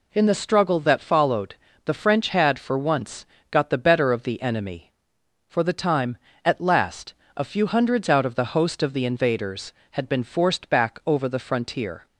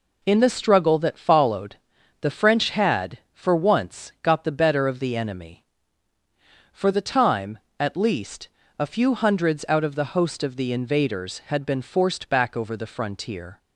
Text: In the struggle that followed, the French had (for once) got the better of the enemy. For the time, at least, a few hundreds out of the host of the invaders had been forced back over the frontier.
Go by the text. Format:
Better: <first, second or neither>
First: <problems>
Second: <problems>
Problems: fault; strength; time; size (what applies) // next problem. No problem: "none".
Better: second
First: says "last" for "least"; at 6.5 s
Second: none